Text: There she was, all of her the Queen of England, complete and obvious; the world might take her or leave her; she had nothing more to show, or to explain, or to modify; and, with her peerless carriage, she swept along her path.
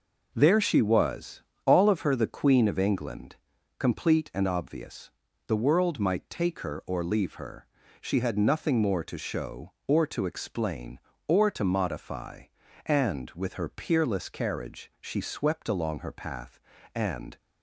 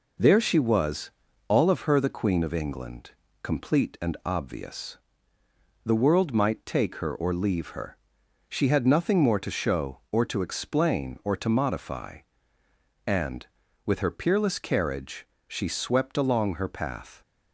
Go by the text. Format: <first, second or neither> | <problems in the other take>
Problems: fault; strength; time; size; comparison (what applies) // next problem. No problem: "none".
second | goes on to say "And"; slight; from 16.9 s on; 0.42 s long